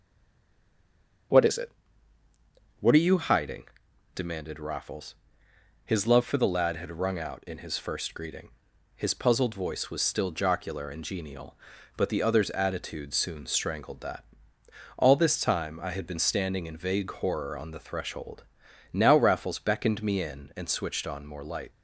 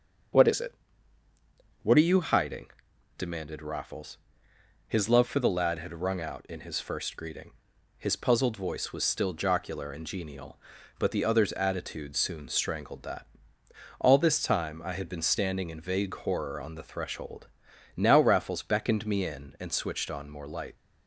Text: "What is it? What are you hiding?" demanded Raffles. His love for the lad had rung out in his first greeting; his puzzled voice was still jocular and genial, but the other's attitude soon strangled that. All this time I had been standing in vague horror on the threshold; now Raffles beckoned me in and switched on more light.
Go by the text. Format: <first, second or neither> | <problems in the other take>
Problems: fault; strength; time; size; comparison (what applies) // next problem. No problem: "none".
second | stays silent before the first word; noticeable; until 1.3 s; 1.3 s long // starts louder than the rest; strong; until 3.4 s; 7 dB; strong in the second